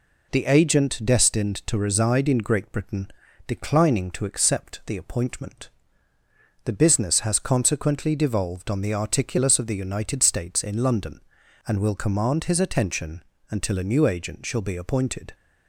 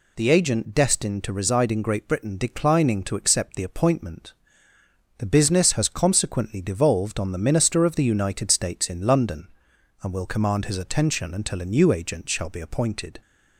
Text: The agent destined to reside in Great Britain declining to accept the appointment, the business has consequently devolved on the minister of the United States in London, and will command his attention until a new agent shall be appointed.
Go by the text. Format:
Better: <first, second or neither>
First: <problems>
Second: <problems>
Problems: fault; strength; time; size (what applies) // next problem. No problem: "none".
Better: second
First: pauses between "Britain" and "declining"; slight; at 3.1 s; 0.36 s long // says "articulus" for "minister"; at 8.9 s // pauses between "attention" and "until"; slight; at 13.2 s; 0.26 s long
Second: none